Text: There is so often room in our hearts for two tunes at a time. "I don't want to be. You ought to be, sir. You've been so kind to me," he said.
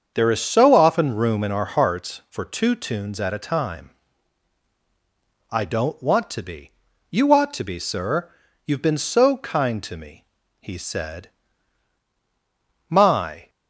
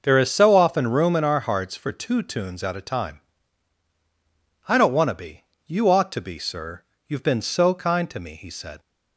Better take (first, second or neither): second